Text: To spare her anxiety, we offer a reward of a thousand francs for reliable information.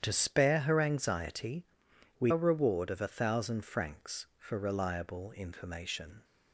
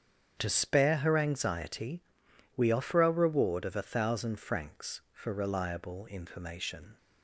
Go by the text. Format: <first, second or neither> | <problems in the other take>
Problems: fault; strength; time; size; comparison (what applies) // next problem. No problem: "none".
second | starts louder than the rest; strong; until 1.0 s; 9 dB; strong in the second // skips "offer"; at 2.3 s